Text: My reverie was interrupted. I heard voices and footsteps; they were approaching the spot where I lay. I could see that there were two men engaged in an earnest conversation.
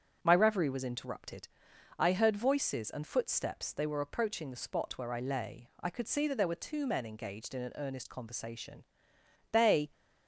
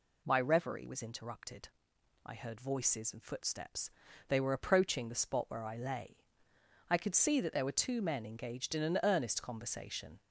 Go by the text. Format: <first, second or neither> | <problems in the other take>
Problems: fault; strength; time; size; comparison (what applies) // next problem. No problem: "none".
second | starts louder than the rest; until 1.2 s; 7 dB // goes on to say "They"; slight; from 9.5 s on; 0.38 s long